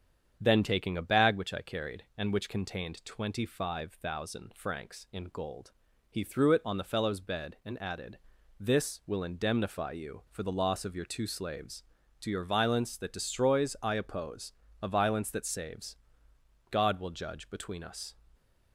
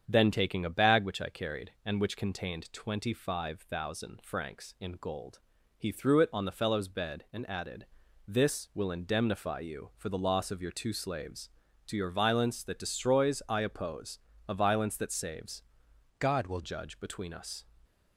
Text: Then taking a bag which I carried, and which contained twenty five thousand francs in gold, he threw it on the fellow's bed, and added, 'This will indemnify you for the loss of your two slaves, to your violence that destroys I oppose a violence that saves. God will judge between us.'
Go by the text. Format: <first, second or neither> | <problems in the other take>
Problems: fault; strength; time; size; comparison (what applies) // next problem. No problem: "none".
first | starts louder than the rest; strong; until 1.0 s; 7.5 dB; strong in the first // pauses between "oppose" and "a"; slight; at 14.1 s; 0.28 s long; slight in the first // changes voice from "God" to "will"; from 16.1 to 16.6 s; 0.5 s long